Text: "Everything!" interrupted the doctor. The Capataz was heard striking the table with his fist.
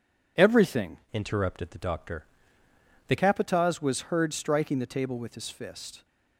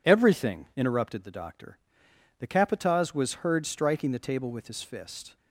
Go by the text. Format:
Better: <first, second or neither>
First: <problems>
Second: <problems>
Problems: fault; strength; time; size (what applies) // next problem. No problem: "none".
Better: second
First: changes voice from "interrupted" to "The"; from 1.1 to 3.1 s; 2.0 s long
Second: none